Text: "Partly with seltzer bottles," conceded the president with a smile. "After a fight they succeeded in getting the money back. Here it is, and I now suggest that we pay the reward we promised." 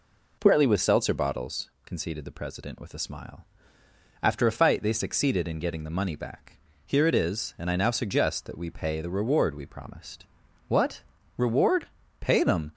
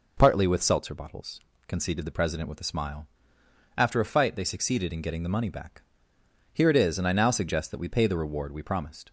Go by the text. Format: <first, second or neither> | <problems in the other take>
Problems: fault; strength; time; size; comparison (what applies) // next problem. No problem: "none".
second | goes on to say "What Reward Pay them"; strong; from 10.6 s on; 2.0 s long